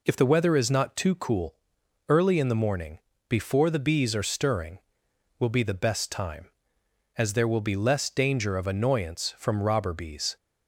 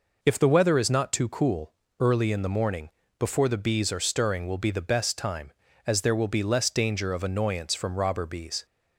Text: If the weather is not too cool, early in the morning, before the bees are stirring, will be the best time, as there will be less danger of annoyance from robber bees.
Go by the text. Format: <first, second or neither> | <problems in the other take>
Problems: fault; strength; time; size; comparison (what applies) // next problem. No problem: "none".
neither | none